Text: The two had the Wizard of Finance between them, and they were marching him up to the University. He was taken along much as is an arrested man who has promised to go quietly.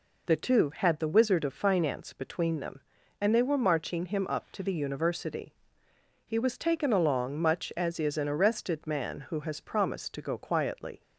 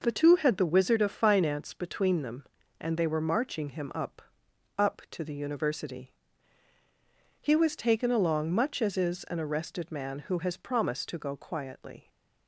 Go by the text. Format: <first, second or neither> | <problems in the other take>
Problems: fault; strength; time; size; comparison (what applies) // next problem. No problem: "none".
first | says "up" twice; at 4.7 s